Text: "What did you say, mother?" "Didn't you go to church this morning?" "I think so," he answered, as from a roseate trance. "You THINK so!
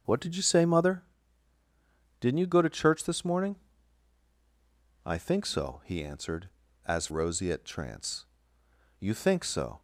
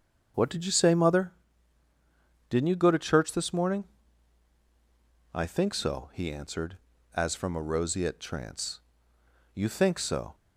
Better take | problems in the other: second | starts louder than the rest; until 2.2 s; 7 dB; also in the second // skips "from a"; at 7.0 s

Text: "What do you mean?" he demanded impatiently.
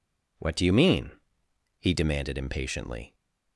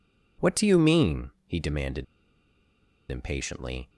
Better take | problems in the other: first | pauses between "demanded" and "impatiently"; at 2.0 s; 1.0 s long

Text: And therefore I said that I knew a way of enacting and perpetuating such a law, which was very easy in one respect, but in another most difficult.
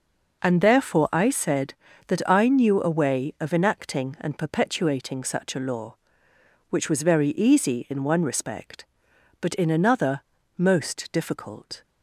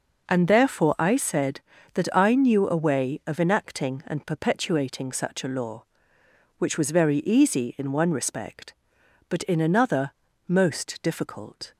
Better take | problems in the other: neither | pauses between "another" and "most"; slight; the same in both

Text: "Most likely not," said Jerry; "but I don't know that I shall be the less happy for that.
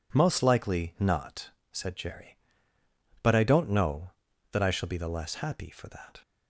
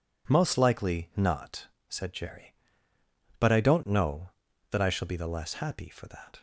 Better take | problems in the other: neither | none

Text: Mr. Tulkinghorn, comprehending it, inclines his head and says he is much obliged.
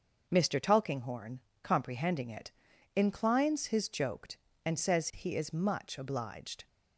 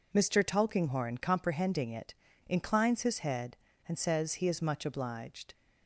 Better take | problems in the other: second | starts louder than the rest; noticeable; until 1.3 s; 6 dB // says "joked" for "head"; at 3.8 s

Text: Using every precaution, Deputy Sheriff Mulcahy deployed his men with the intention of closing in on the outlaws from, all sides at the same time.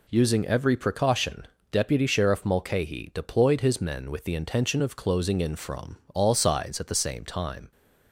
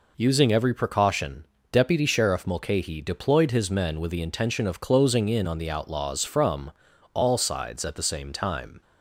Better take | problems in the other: second | skips "on the outlaws"; at 5.5 s

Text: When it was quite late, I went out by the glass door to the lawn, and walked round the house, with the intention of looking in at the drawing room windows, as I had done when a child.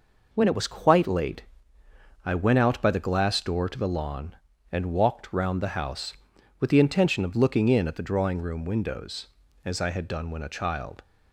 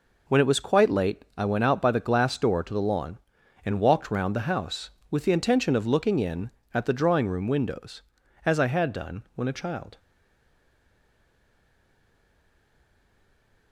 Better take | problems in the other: first | stays silent after the last word; strong; from 9.9 s on; 3.8 s long

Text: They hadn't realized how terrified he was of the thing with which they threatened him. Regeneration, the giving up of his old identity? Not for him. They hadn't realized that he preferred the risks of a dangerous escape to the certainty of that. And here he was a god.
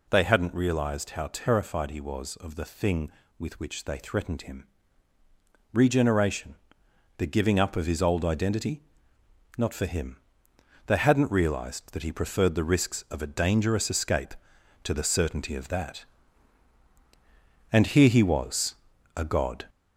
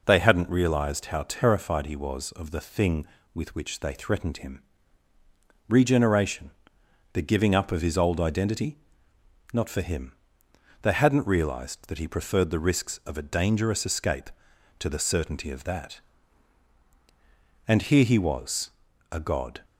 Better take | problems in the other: second | gets louder; noticeable; throughout; 4 dB // pauses between "was" and "a"; at 18.7 s; 0.40 s long; also in the second

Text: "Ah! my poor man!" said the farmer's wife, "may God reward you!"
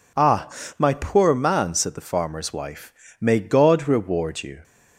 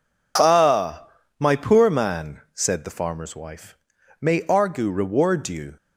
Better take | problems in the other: first | says "Argu" for "God"; at 4.4 s

